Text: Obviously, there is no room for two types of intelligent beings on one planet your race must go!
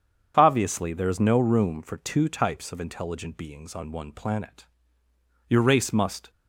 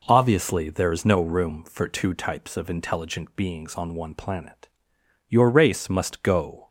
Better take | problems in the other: second | starts louder than the rest; strong; until 1.3 s; 7.5 dB // pauses between "planet" and "your"; noticeable; at 4.6 s; 0.84 s long; noticeable in the second // stops before "go"; at 6.2 s

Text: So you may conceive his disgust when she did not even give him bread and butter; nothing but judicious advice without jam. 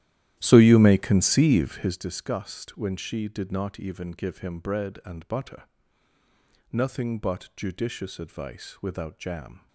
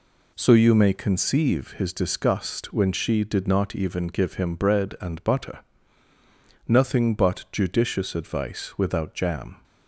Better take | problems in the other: second | starts louder than the rest; strong; until 2.1 s; 13 dB

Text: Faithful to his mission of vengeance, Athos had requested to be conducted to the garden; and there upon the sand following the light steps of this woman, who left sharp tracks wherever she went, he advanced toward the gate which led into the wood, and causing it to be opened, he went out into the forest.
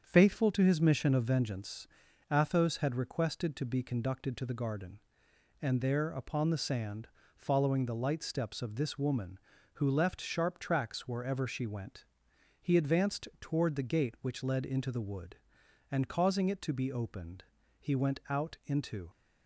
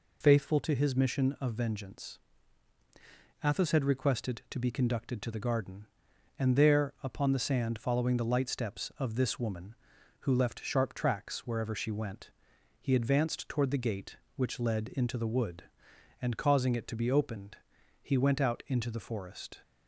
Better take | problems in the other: second | starts louder than the rest; strong; until 1.0 s; 7 dB // pauses between "sand" and "following"; slight; at 7.0 s; 0.28 s long // stops before "the forest"; at 19.0 s

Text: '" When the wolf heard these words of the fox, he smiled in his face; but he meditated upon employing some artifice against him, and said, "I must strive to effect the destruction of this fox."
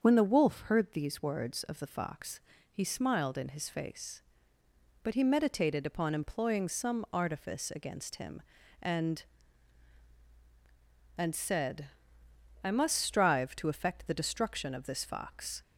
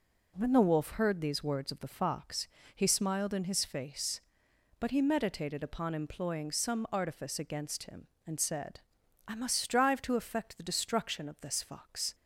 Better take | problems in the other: second | starts louder than the rest; until 1.0 s; 7 dB // says "and" twice; at 11.1 s

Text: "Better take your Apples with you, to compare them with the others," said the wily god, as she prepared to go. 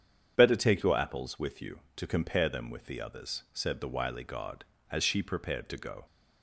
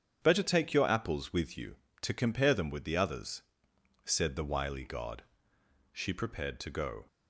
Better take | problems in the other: first | starts louder than the rest; strong; until 1.2 s; 8 dB; strong in the first // skips "as"; at 5.5 s

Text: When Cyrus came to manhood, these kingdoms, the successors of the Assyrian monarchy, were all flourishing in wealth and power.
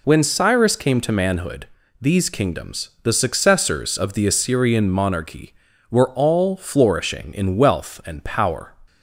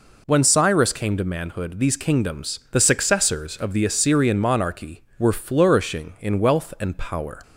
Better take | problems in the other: first | skips "all"; at 5.3 s

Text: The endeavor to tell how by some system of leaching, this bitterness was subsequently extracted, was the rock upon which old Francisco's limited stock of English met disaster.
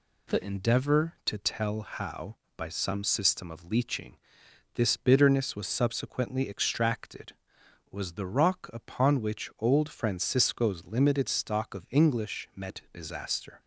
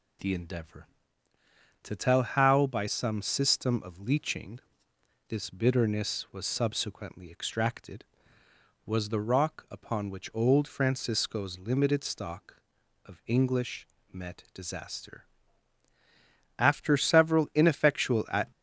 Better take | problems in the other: first | pauses between "English" and "met"; slight; at 13.8 s; 0.26 s long // goes on to say "After several ineffectual at"; strong; from 16.5 s on; 1.9 s long

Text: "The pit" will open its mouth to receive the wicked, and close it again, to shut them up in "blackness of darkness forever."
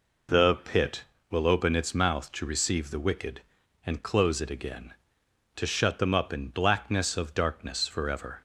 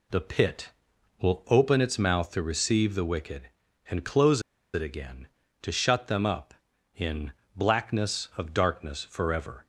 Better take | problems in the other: first | pauses between "close" and "it"; slight; at 4.3 s; 0.34 s long // pauses between "in" and "blackness"; slight; at 7.3 s; 0.24 s long

